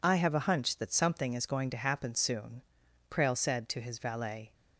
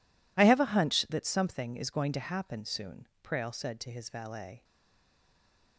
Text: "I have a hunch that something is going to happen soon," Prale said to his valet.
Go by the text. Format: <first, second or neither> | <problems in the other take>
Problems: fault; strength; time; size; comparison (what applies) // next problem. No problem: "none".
first | stays silent after the last word; noticeable; from 4.6 s on; 1.1 s long